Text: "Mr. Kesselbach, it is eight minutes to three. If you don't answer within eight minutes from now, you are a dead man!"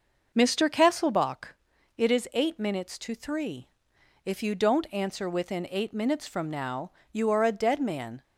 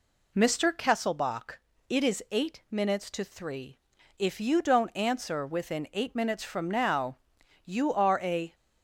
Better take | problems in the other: first | stops before "dead man"; at 8.5 s

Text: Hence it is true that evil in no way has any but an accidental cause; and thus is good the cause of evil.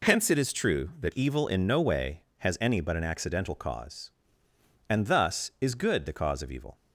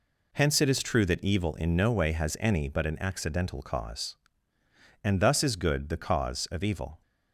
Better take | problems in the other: neither | none

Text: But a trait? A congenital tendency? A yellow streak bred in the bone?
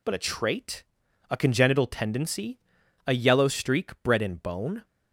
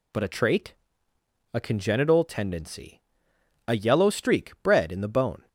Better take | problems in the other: second | skips "the"; at 4.3 s

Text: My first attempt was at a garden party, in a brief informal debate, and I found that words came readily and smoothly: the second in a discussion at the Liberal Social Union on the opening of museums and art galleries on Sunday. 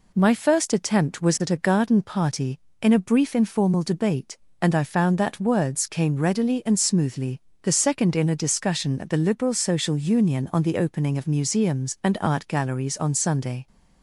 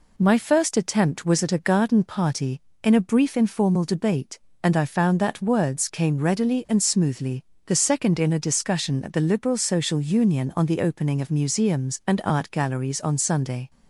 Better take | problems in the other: neither | none

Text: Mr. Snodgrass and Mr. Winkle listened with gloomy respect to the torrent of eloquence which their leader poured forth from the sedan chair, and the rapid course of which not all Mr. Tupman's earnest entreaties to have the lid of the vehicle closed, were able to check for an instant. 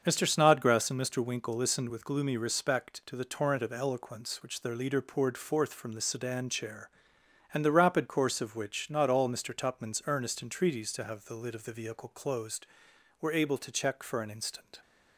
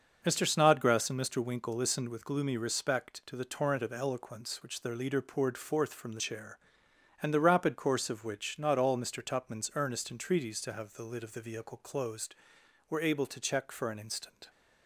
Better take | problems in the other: first | starts louder than the rest; until 1.2 s; 6 dB; also in the first // skips "sedan"; at 6.1 s

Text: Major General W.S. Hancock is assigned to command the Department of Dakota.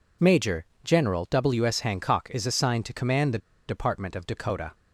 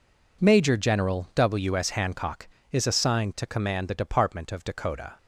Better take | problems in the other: second | pauses between "Major" and "General"; slight; at 0.6 s; 0.18 s long // pauses between "the" and "Department"; slight; at 3.3 s; 0.29 s long

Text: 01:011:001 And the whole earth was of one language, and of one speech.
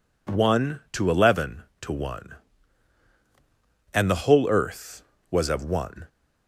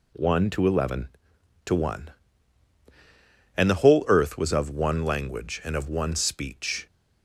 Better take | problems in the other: second | stops before "language and of one speech"; at 6.0 s

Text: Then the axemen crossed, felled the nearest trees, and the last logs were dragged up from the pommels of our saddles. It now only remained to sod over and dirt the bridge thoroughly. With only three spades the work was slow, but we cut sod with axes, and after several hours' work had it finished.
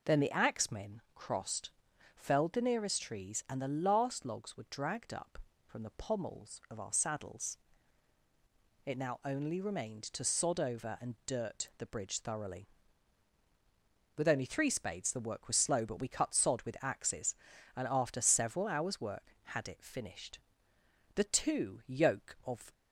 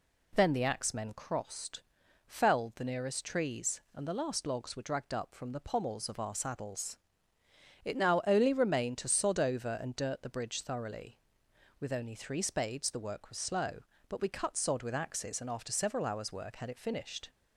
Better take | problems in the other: second | goes on to say "The two yoke of"; from 21.1 s on; 1.5 s long

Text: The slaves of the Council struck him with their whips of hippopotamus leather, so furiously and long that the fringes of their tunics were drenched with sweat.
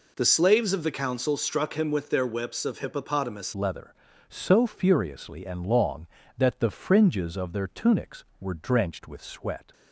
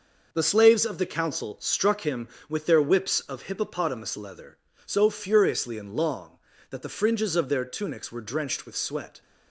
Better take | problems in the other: second | changes voice at "leather"; from 3.5 s on; 6.2 s long

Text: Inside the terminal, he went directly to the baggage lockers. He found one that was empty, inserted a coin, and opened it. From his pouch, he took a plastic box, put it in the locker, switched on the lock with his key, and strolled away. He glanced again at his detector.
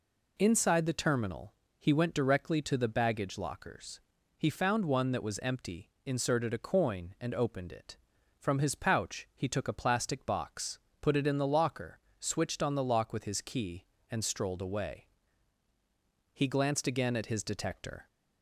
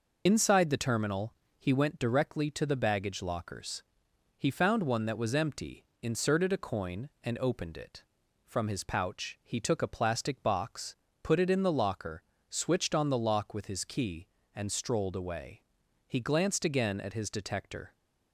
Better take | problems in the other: first | loses the start of "Inside"; at 0.2 s; 60 ms

